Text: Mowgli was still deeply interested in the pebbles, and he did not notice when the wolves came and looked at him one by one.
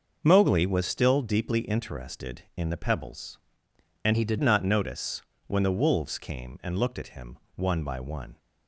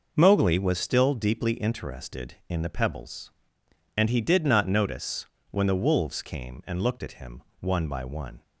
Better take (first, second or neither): second